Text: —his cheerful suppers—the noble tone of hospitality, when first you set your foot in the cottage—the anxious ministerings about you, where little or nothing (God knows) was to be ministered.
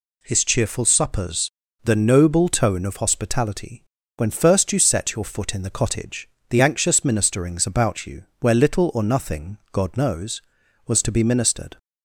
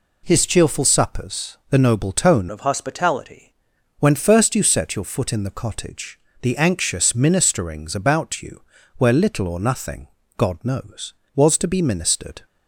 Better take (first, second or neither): first